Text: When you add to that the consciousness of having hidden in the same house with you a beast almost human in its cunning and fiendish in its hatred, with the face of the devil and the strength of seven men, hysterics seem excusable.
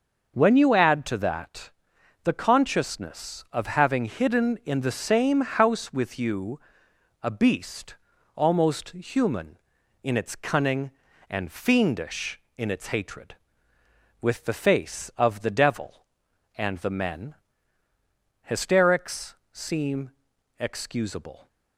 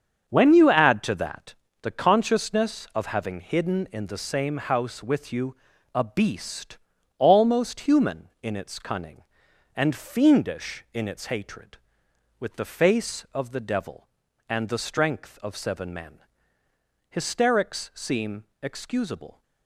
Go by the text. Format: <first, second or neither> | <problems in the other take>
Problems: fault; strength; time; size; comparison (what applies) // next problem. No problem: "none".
second | starts louder than the rest; until 1.3 s; 6 dB; strong in the second // pauses between "that" and "the"; noticeable; at 1.7 s; 0.54 s long; slight in the second // pauses between "you" and "a"; noticeable; at 6.5 s; 0.62 s long; also in the second // pauses between "beast" and "almost"; at 7.9 s; 0.42 s long; also in the second // skips "strength of seven"; at 16.9 s // pauses between "hysterics" and "seem"; slight; at 19.3 s; 0.16 s long // pauses between "seem" and "excusable"; noticeable; at 20.0 s; 0.50 s long; slight in the second